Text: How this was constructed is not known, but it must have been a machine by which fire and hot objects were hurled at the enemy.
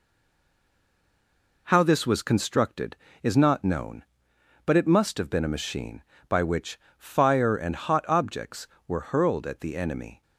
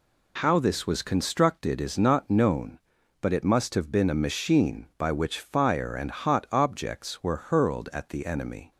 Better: second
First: stays silent before the first word; noticeable; until 1.6 s; 1.6 s long // pauses between "which" and "fire"; slight; at 6.7 s; 0.20 s long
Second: none

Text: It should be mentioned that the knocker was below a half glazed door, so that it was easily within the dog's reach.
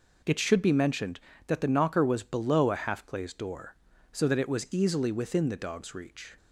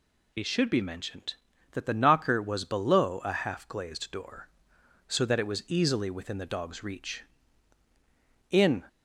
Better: first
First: none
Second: goes on to say "In"; slight; from 8.5 s on; 0.32 s long

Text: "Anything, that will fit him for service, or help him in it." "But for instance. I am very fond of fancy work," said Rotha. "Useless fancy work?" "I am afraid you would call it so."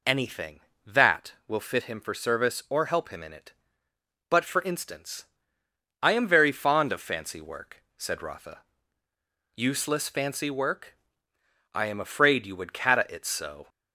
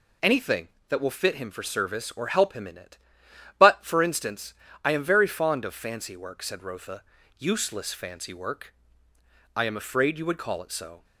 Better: second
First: says "cata" for "call"; at 12.7 s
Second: none

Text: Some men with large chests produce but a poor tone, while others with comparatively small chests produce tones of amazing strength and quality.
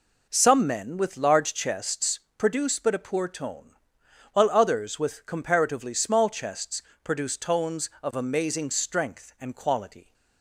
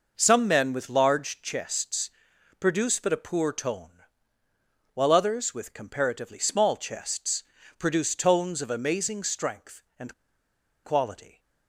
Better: first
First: pauses between "chests" and "produce"; slight; at 2.1 s; 0.16 s long // pauses between "chests" and "produce"; slight; at 6.8 s; 0.20 s long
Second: pauses between "chests" and "produce"; noticeable; at 2.0 s; 0.50 s long // pauses between "chests" and "produce"; slight; at 7.4 s; 0.36 s long // pauses between "and" and "quality"; noticeable; at 10.1 s; 0.71 s long

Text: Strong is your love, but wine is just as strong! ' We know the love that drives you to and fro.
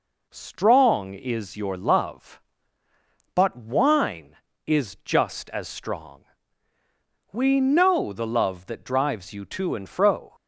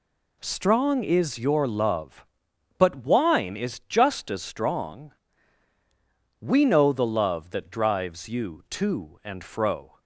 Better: neither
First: none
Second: none

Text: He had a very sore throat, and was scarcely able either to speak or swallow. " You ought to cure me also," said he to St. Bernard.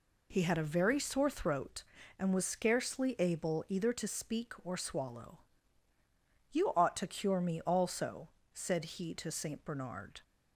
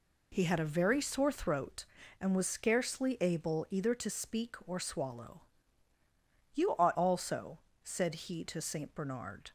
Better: first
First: none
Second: skips "to cure me"; at 6.9 s

